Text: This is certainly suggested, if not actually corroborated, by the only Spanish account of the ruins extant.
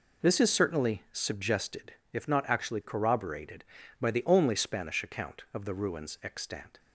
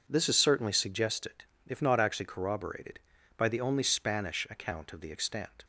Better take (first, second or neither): first